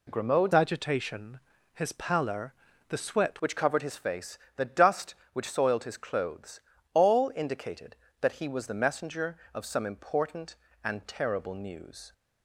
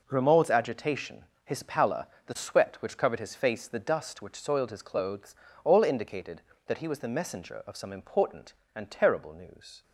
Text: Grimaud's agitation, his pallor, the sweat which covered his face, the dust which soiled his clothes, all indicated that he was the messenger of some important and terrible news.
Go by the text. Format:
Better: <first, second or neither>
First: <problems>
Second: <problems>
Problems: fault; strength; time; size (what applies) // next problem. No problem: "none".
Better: second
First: changes voice from "agitation" to "sweat"; from 0.5 to 3.3 s; 2.8 s long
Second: none